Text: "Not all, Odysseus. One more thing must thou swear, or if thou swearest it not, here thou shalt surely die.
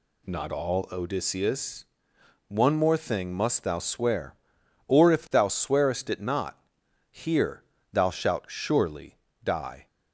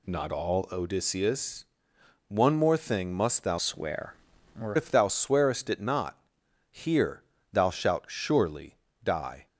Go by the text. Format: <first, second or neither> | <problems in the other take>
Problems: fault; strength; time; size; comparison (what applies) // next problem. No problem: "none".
first | changes voice from "swear" to "or"; from 3.5 to 4.7 s; 1.2 s long // pauses between "here" and "thou"; slight; at 7.2 s; 0.30 s long; slight in the first // pauses between "surely" and "die"; slight; at 8.7 s; 0.26 s long; slight in the first